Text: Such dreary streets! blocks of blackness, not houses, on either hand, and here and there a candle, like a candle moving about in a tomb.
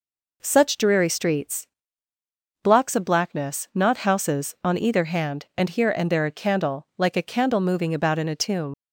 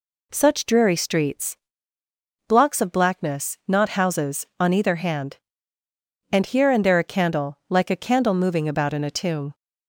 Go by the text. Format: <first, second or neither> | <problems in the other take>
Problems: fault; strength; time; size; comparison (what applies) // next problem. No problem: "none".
second | leaves "tomb" unfinished; at 8.7 s; 80 ms